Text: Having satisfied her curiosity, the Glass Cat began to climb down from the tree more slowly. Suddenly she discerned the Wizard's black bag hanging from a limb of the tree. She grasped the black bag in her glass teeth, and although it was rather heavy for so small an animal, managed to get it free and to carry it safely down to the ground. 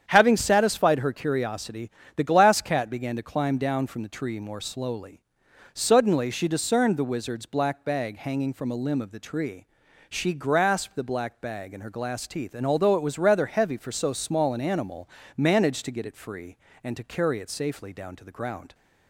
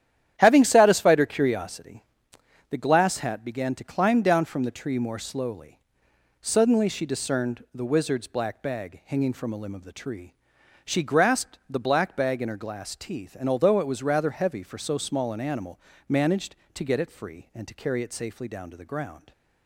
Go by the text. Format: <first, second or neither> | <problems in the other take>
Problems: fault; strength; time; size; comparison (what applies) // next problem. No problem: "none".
first | starts louder than the rest; strong; until 1.4 s; 10.5 dB; strong in the first // says "Hat" for "Cat"; at 3.1 s